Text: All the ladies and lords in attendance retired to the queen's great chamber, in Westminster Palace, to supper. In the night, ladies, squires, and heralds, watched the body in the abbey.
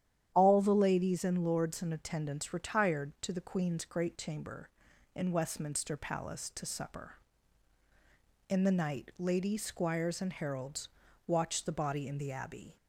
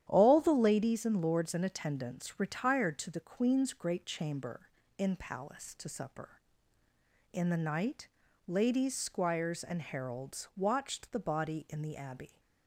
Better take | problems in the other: first | starts louder than the rest; strong; until 1.1 s; 10.5 dB; strong in the first // skips "Westminster"; at 5.1 s

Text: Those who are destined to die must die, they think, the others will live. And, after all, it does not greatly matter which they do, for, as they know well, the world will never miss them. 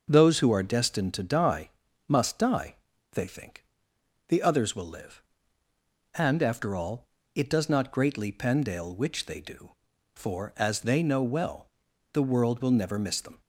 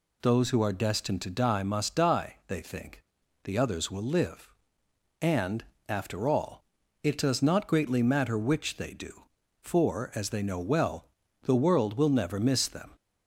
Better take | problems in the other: second | starts louder than the rest; until 1.1 s; 6.5 dB // pauses between "die" and "must"; at 1.6 s; 0.38 s long // says "pendale" for "matter"; at 8.3 s

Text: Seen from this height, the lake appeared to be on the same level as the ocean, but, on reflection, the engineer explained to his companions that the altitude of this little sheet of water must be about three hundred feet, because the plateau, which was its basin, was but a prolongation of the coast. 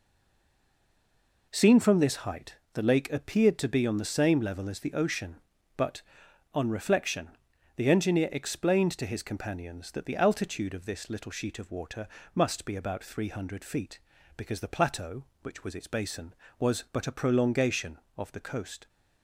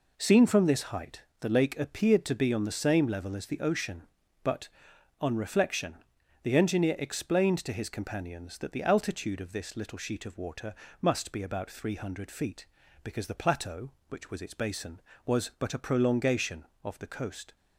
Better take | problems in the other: second | stays silent before the first word; noticeable; until 1.5 s; 1.5 s long // pauses between "water" and "must"; slight; at 12.0 s; 0.28 s long; slight in the second

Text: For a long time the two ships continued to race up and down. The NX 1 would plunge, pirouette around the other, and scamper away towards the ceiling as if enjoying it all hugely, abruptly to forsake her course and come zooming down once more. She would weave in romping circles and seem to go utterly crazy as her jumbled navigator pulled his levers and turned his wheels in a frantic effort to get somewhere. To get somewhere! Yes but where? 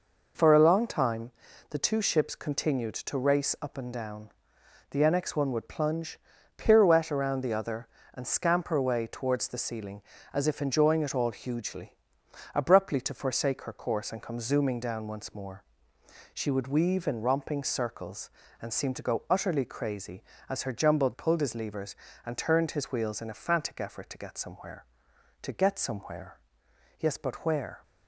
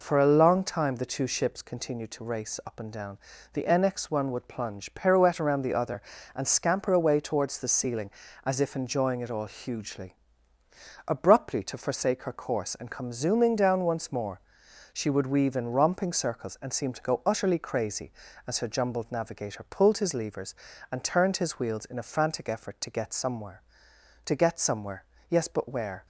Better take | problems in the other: second | pauses between "time" and "the"; at 1.3 s; 0.40 s long // skips "navigator"; at 21.1 s

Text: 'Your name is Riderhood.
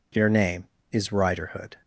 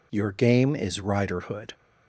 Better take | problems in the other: first | says "game" for "name"; at 0.3 s

